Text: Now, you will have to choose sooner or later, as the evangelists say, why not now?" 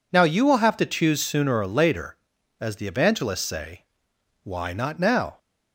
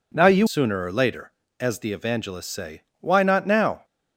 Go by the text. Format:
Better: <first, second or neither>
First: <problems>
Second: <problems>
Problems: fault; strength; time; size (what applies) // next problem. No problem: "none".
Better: first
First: none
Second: skips "will have to choose"; at 0.4 s